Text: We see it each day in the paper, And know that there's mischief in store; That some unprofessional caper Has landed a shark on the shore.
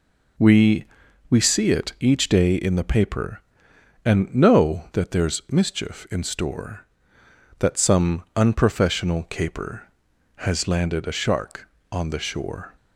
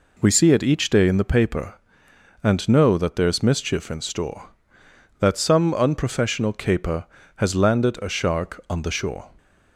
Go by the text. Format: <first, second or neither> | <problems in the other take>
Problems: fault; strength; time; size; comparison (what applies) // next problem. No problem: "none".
second | says "We" twice; at 1.2 s